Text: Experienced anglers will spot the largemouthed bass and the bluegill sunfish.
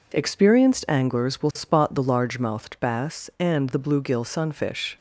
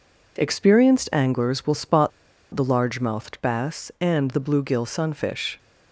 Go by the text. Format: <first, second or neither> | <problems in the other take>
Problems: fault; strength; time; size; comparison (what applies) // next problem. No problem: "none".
first | pauses between "spot" and "the"; at 2.1 s; 0.43 s long